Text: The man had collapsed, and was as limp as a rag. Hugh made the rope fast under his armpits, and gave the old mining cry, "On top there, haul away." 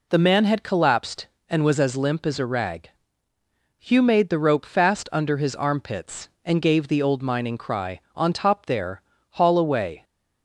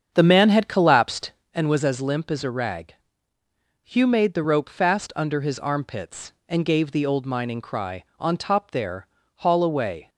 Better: first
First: none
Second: starts louder than the rest; strong; until 1.6 s; 7.5 dB

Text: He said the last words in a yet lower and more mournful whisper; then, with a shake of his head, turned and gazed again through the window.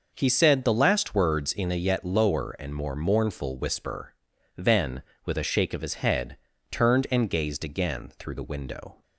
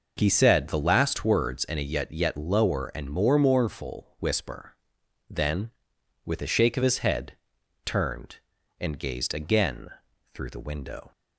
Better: first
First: none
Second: says "yet" twice; at 2.0 s // pauses between "again" and "through"; at 9.8 s; 0.44 s long

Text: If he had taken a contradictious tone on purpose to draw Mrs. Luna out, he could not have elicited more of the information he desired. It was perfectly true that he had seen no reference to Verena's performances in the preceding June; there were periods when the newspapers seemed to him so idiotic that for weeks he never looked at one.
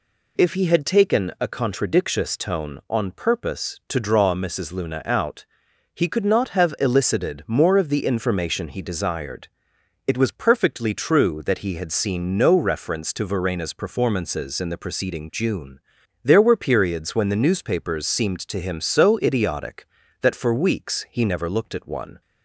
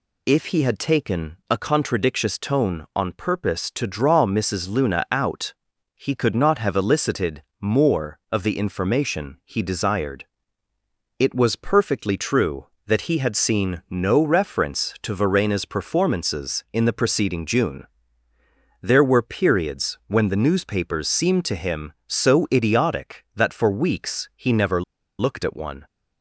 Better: first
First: none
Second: pauses between "elicited" and "more"; slight; at 7.4 s; 0.16 s long // pauses between "never" and "looked"; at 24.8 s; 0.36 s long

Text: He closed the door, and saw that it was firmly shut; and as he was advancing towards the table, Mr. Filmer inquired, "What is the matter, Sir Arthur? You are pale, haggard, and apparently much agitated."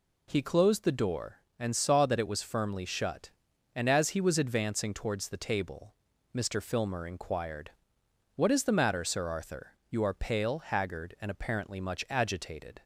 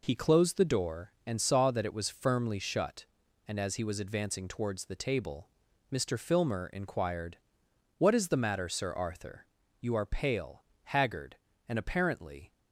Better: first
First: none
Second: stops before "much agitated"; at 12.5 s

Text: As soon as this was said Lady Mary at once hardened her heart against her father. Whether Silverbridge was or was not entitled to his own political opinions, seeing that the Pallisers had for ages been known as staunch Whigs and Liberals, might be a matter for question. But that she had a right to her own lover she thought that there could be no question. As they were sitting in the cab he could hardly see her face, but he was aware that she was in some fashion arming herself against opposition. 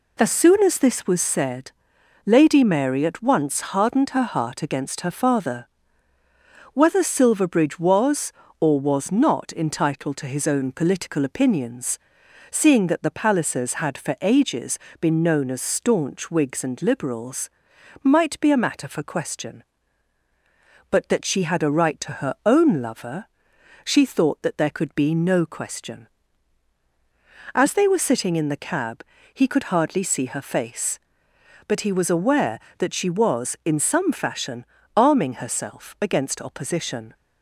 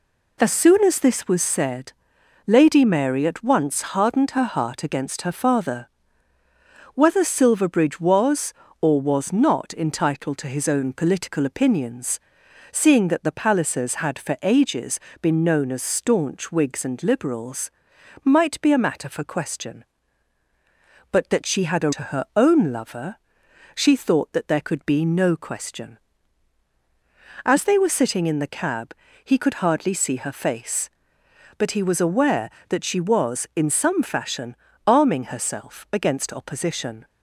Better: first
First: pauses between "said" and "Lady"; noticeable; at 1.6 s; 0.56 s long // pauses between "ages" and "been"; slight; at 14.7 s; 0.24 s long // pauses between "lover" and "she"; noticeable; at 23.2 s; 0.58 s long // pauses between "cab" and "he"; slight; at 29.0 s; 0.28 s long // pauses between "fashion" and "arming"; slight; at 34.6 s; 0.30 s long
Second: pauses between "said" and "Lady"; noticeable; at 1.9 s; 0.56 s long // pauses between "ages" and "been"; slight; at 14.9 s; 0.24 s long // skips "right"; at 21.9 s // pauses between "lover" and "she"; noticeable; at 23.1 s; 0.58 s long // pauses between "cab" and "he"; slight; at 28.9 s; 0.28 s long // pauses between "fashion" and "arming"; slight; at 34.5 s; 0.30 s long

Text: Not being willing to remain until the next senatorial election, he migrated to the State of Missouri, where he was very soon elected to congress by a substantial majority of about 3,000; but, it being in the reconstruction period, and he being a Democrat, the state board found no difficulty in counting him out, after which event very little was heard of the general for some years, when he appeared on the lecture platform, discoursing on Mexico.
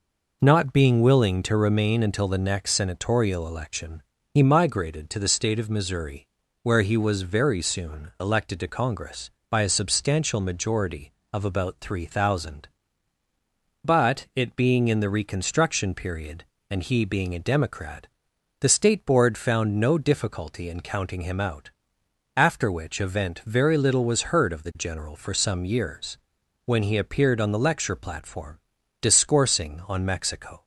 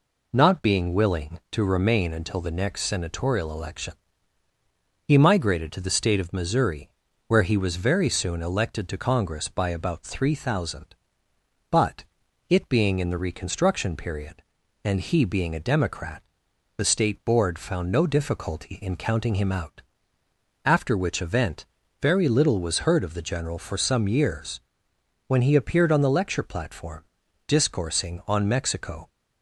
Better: first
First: none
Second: skips "a substantial majority of"; at 9.6 s // pauses between "event" and "very"; slight; at 21.6 s; 0.36 s long

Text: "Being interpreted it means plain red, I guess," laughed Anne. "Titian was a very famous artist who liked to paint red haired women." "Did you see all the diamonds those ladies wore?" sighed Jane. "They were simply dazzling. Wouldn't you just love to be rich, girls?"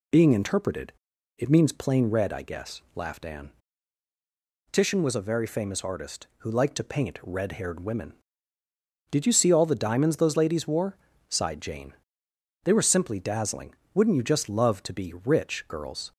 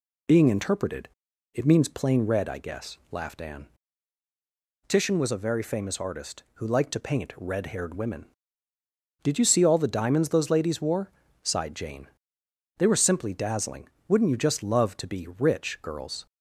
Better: neither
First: pauses between "interpreted" and "it"; noticeable; at 0.9 s; 0.46 s long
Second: pauses between "interpreted" and "it"; noticeable; at 1.0 s; 0.46 s long

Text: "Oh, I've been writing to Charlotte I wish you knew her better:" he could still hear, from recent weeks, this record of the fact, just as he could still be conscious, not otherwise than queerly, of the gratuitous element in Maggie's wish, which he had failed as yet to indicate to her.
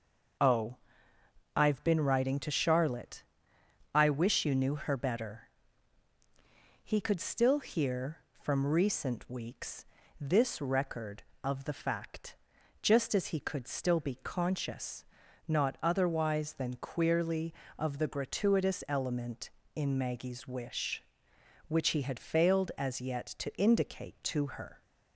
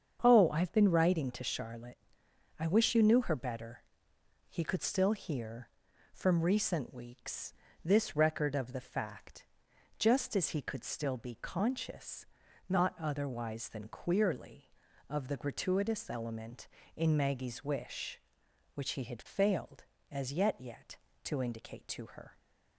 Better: first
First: starts louder than the rest; noticeable; until 2.2 s; 6 dB // pauses between "Charlotte" and "I"; noticeable; at 3.2 s; 0.68 s long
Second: starts louder than the rest; strong; until 1.2 s; 7.5 dB // pauses between "Charlotte" and "I"; noticeable; at 1.9 s; 0.62 s long // says "yet" twice; at 20.5 s

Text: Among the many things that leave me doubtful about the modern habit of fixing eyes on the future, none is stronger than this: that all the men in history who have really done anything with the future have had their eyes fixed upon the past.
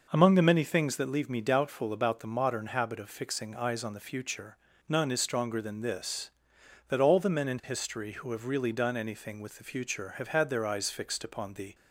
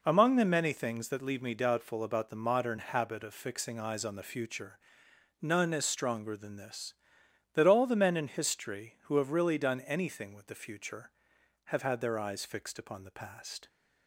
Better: second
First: stops before "past"; at 11.7 s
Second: none

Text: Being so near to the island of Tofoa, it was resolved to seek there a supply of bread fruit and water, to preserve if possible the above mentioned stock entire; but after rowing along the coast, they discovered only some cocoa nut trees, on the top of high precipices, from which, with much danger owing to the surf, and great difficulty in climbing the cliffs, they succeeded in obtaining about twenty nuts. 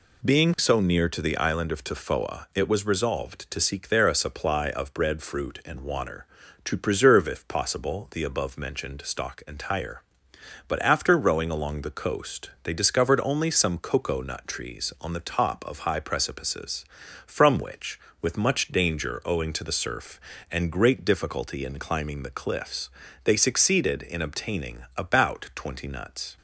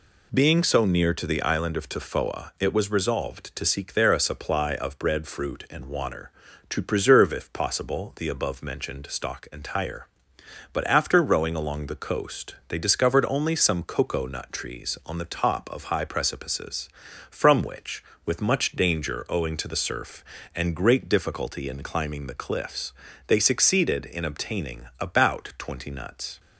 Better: neither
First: none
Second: none

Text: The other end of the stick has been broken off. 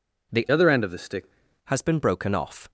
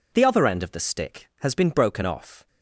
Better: second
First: changes voice from "other" to "stick"; from 0.5 to 1.3 s; 0.8 s long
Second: none

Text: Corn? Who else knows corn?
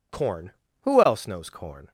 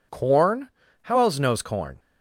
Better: first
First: none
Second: says "How" for "Who"; at 1.0 s

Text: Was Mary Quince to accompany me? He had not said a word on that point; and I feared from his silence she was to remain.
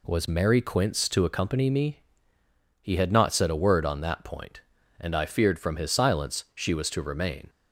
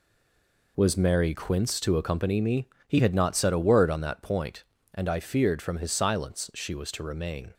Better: first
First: none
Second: stays silent before the first word; slight; until 0.7 s; 0.7 s long

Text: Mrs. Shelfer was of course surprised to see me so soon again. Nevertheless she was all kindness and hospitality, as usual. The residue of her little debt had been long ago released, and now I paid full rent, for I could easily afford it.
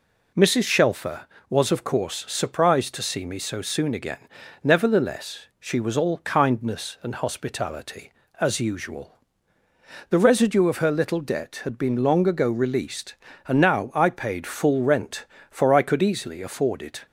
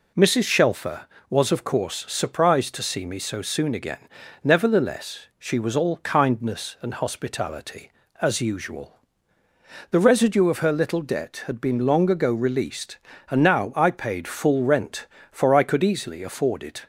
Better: neither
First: none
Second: none

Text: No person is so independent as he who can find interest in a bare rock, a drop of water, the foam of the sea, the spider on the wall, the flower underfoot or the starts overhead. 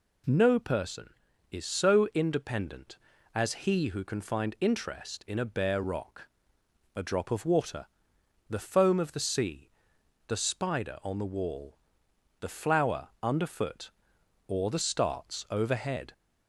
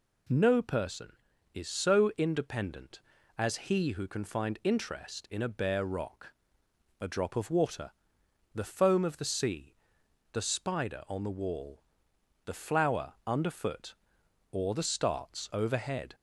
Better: neither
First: none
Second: none

